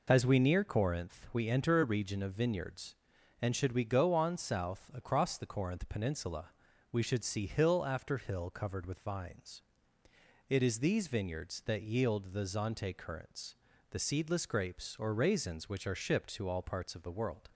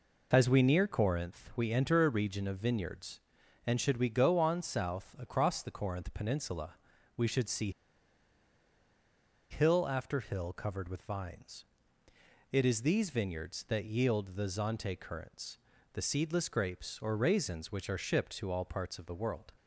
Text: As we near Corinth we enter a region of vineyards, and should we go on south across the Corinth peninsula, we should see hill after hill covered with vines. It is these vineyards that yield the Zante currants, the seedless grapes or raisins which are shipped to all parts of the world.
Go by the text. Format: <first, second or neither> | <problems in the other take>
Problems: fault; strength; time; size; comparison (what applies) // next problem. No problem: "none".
first | pauses between "see" and "hill"; strong; at 7.6 s; 1.8 s long